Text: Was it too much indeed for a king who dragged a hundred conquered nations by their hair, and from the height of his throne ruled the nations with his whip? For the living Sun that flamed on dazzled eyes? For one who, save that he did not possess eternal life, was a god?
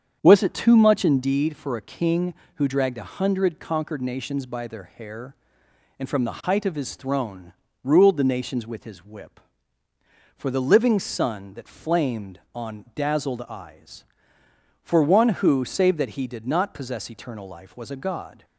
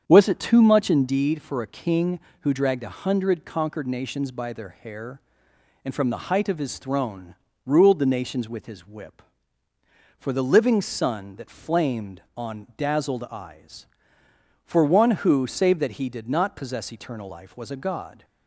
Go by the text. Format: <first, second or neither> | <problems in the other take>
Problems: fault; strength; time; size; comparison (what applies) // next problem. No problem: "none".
neither | starts louder than the rest; strong; the same in both // pauses between "throne" and "ruled"; slight; the same in both